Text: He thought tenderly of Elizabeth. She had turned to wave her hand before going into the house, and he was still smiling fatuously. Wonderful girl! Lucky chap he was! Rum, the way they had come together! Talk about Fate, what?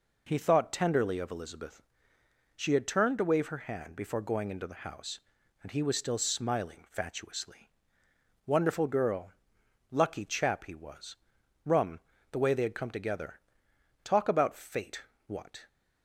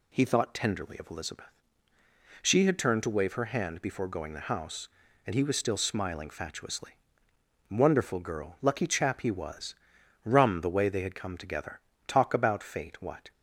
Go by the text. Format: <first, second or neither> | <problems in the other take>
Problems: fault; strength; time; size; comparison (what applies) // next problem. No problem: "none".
first | skips "into"; at 4.3 s